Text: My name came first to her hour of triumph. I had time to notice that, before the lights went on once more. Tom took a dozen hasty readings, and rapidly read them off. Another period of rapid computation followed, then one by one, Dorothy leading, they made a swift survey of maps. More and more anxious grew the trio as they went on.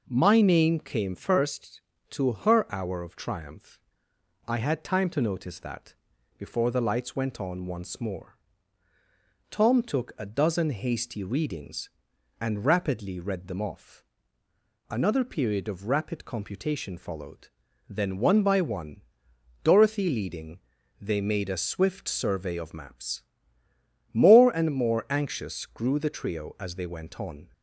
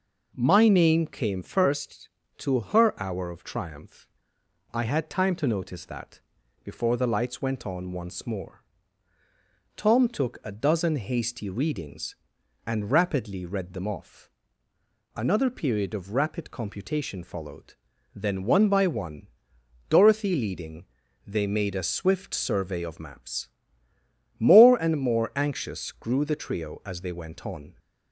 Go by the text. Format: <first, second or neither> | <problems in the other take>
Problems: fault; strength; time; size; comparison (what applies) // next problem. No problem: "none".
neither | none